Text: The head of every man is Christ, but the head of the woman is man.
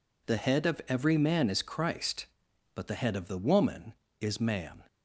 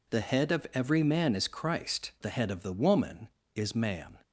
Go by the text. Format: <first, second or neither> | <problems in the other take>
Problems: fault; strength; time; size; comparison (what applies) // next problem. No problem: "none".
first | skips "but"; at 2.1 s